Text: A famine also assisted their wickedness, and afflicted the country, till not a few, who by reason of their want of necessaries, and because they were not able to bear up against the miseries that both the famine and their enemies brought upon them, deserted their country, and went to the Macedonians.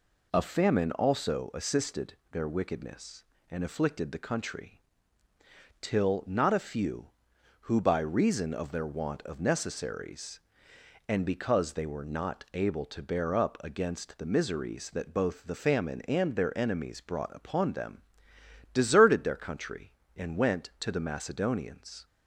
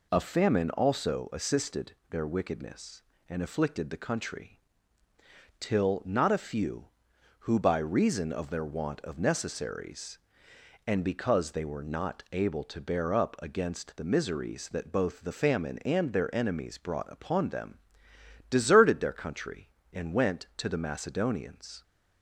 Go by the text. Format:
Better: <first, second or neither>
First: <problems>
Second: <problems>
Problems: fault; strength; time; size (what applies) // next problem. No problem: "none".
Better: neither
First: pauses between "assisted" and "their"; slight; at 2.1 s; 0.16 s long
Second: pauses between "assisted" and "their"; slight; at 1.9 s; 0.16 s long